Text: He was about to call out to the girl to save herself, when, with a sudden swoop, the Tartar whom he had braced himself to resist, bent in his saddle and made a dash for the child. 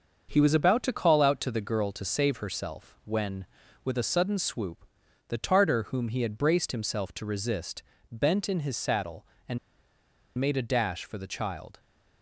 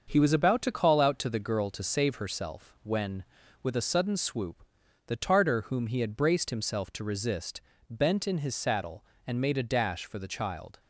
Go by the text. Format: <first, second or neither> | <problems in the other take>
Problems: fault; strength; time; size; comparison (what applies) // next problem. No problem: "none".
second | starts louder than the rest; until 1.3 s; 6.5 dB; also in the second // pauses between "and" and "made"; noticeable; at 9.5 s; 0.79 s long